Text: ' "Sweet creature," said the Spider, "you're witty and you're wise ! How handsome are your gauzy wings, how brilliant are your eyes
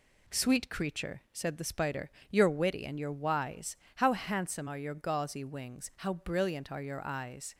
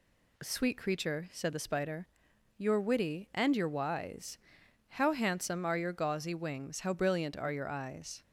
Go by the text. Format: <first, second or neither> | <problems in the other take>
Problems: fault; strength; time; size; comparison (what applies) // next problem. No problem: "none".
neither | none